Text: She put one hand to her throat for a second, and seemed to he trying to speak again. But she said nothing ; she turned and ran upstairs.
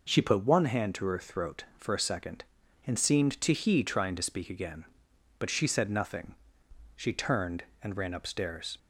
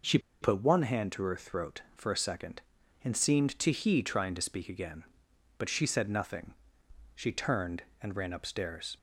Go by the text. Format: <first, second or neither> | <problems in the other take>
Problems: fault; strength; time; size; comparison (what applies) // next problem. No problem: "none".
first | pauses between "She" and "put"; slight; at 0.1 s; 0.23 s long